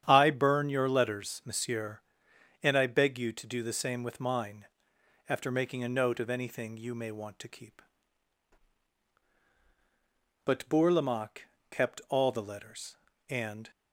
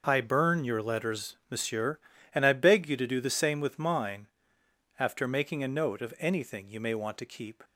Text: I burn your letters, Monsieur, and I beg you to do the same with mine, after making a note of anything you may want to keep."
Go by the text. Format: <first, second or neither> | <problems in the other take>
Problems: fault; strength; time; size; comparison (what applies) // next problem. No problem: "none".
second | starts louder than the rest; strong; until 1.0 s; 9 dB // goes on to say "But Bourlamaque kept all the letters and"; strong; from 10.4 s on; 3.2 s long